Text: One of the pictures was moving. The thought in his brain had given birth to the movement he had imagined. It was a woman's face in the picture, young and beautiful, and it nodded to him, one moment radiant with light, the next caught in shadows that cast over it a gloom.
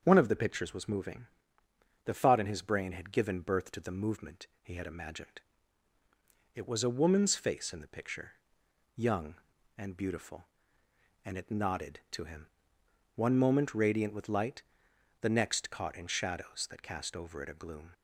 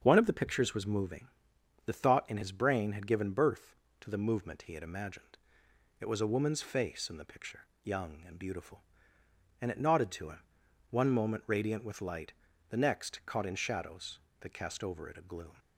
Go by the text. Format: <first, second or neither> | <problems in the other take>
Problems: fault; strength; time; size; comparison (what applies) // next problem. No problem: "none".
neither | starts louder than the rest; the same in both